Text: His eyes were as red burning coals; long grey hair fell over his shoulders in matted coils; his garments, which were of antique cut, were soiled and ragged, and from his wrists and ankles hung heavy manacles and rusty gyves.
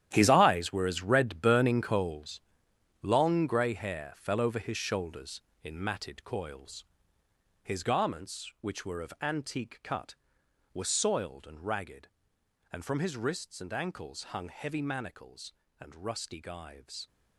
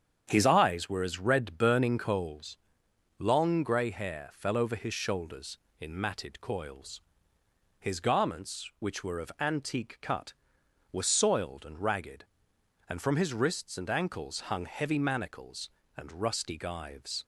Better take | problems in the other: second | gets quieter; strong; throughout; 13 dB // starts louder than the rest; strong; until 1.1 s; 11 dB; strong in the second

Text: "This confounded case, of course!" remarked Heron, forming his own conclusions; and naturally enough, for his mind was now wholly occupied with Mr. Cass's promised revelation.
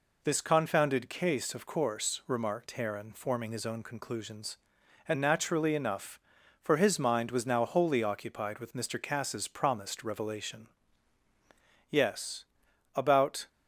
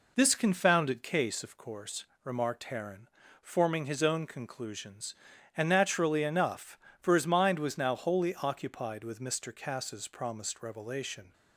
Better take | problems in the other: second | goes on to say "Yes about"; from 11.8 s on; 1.5 s long

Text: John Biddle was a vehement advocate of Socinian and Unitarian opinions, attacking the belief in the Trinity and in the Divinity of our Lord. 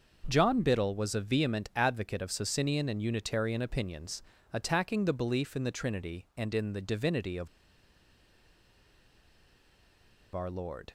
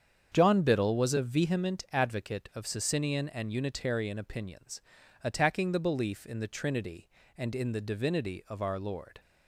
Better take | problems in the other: second | starts louder than the rest; until 1.2 s; 6 dB; strong in the second // pauses between "of" and "our"; strong; at 7.4 s; 2.8 s long

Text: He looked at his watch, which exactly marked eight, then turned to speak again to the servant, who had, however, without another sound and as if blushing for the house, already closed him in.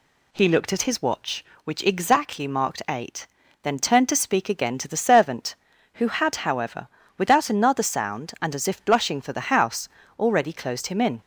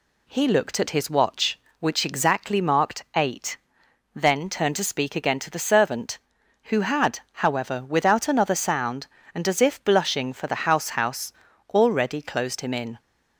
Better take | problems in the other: first | says "house" twice; at 10.9 s

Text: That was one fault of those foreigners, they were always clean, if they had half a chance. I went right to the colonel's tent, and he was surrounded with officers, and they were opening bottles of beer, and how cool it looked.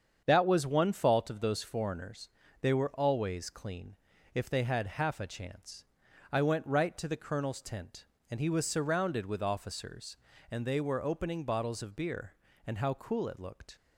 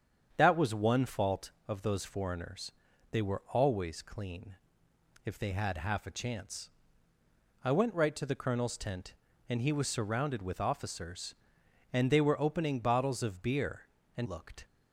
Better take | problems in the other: first | starts louder than the rest; strong; until 1.3 s; 7.5 dB; strong in the first // skips "how cool it"; at 14.2 s

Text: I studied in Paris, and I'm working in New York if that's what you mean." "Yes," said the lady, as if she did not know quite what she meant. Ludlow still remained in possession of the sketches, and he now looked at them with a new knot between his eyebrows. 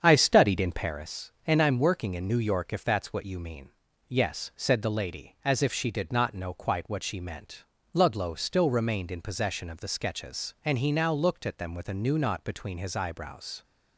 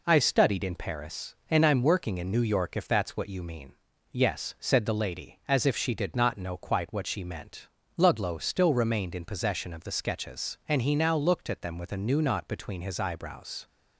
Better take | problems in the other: second | starts louder than the rest; strong; until 1.0 s; 7.5 dB

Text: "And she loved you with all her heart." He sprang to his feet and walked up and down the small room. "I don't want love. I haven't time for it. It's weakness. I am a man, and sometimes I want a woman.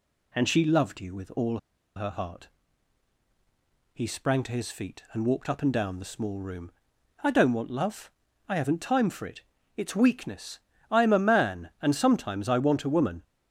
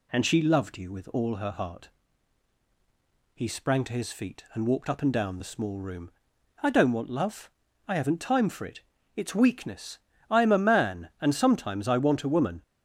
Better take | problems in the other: second | pauses between "all" and "her"; at 1.5 s; 0.37 s long

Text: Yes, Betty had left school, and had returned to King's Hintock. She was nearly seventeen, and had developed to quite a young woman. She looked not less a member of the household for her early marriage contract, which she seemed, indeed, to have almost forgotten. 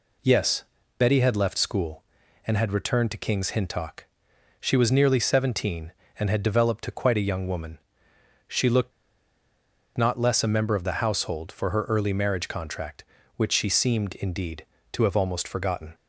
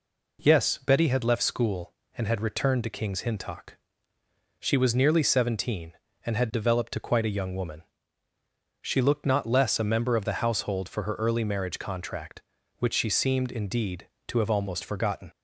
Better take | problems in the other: second | pauses between "looked" and "not"; at 8.9 s; 1.0 s long

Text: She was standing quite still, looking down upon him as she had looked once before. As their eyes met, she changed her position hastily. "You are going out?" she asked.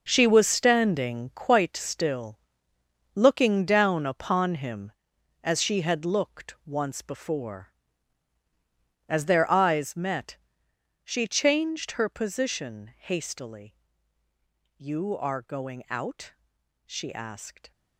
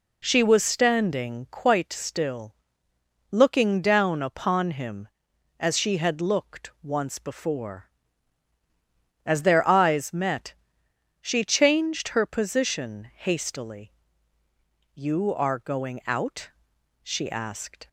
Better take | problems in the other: second | gets quieter; strong; throughout; 11.5 dB

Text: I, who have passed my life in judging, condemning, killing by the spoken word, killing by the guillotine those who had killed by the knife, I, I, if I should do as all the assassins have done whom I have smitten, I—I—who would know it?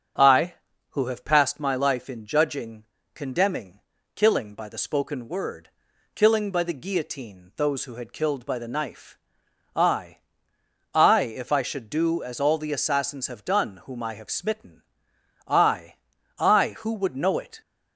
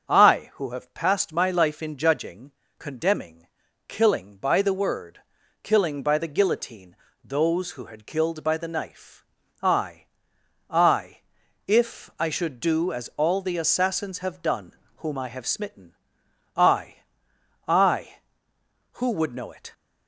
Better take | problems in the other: first | starts louder than the rest; until 1.1 s; 7 dB; strong in the first // skips "spoken"; at 4.7 s // pauses between "guillotine" and "those"; slight; at 6.9 s; 0.28 s long // pauses between "done" and "whom"; slight; at 14.7 s; 0.24 s long

